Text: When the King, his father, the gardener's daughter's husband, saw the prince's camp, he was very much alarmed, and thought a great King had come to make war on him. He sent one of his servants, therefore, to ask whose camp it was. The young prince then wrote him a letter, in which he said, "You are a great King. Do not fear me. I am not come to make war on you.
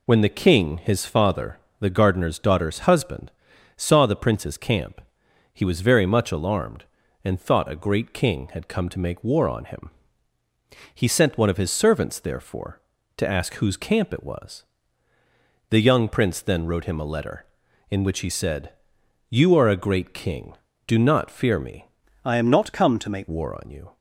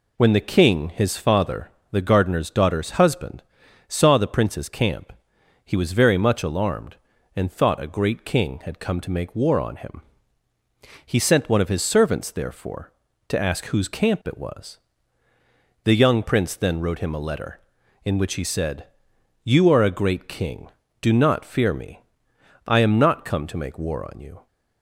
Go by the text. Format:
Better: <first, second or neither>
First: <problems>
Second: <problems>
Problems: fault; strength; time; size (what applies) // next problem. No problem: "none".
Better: second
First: changes voice from "I" to "make"; from 22.2 to 23.2 s; 1.0 s long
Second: none